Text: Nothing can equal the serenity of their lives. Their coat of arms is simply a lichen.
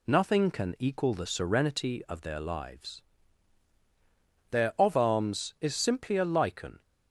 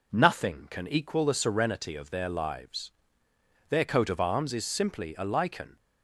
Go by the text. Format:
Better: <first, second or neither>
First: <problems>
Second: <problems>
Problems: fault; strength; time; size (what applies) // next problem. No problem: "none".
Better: second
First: skips "coat"; at 4.7 s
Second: none